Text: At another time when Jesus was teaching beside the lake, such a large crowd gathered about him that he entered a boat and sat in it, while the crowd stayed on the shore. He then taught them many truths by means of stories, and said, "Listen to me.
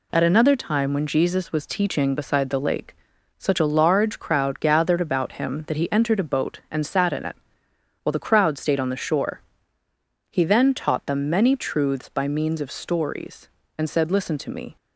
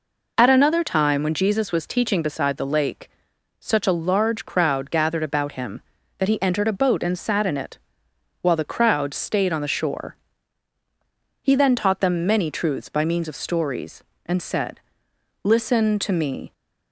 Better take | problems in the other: neither | none

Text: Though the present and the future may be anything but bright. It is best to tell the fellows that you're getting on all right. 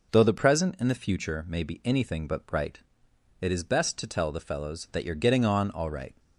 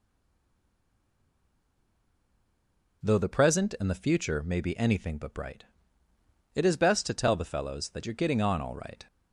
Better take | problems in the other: first | stays silent before the first word; strong; until 3.0 s; 3.0 s long

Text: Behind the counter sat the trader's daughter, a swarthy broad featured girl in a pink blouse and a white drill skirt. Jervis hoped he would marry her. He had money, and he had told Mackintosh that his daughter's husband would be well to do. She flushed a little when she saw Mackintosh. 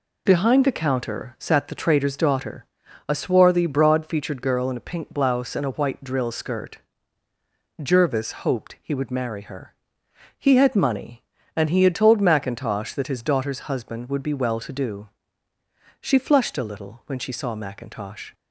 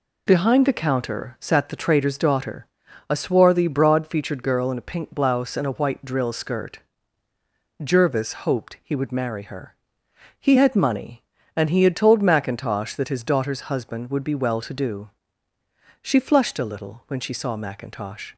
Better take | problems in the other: neither | none

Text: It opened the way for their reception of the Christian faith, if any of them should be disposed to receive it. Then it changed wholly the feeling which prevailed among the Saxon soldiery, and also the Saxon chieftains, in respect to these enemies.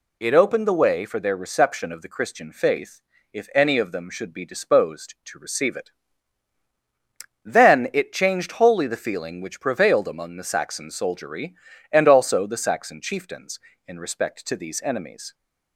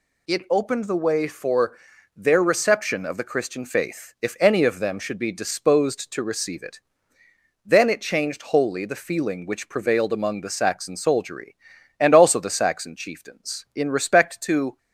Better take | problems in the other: first | pauses between "for" and "their"; at 1.7 s; 0.40 s long // stops before "these enemies"; at 14.7 s

